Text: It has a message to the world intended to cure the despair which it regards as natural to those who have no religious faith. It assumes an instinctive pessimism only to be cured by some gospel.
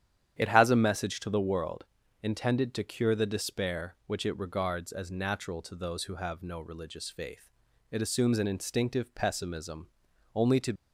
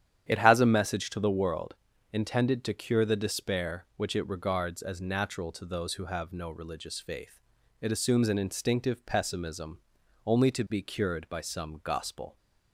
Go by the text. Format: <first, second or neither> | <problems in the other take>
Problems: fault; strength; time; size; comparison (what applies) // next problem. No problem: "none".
second | starts louder than the rest; strong; until 1.4 s; 10 dB; strong in the second // pauses between "world" and "intended"; slight; at 1.8 s; 0.36 s long; slight in the second // pauses between "pessimism" and "only"; noticeable; at 9.8 s; 0.46 s long; noticeable in the second // stops before "be cured by some gospel"; at 10.7 s